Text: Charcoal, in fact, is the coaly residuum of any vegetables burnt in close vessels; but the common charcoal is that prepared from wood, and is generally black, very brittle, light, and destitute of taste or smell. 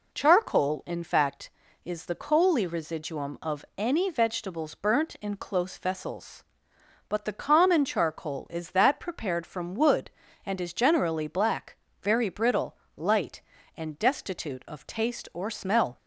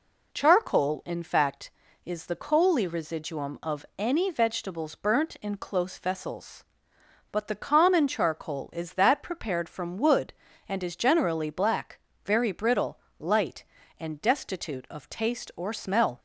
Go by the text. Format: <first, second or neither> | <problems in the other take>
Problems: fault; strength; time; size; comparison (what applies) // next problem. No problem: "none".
neither | none